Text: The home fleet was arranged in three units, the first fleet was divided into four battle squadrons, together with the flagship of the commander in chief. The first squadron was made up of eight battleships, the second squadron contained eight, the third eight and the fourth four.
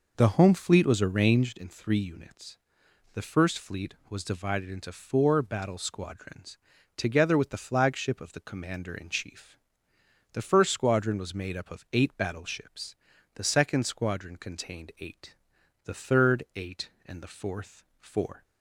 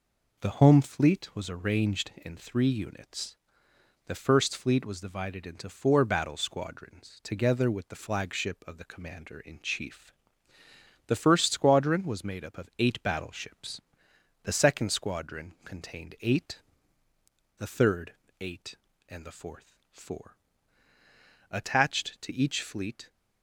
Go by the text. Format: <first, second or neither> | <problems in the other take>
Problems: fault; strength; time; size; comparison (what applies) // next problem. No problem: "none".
first | pauses between "third" and "eight"; slight; at 18.1 s; 0.28 s long // pauses between "fourth" and "four"; slight; at 19.7 s; 0.18 s long; slight in the first // goes on to say "Attached to each fleet"; from 21.5 s on; 1.5 s long